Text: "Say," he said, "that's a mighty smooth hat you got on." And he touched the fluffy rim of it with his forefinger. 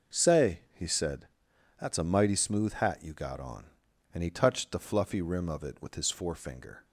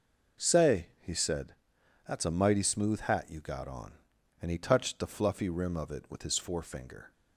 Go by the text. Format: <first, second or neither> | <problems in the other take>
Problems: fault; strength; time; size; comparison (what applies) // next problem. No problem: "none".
neither | none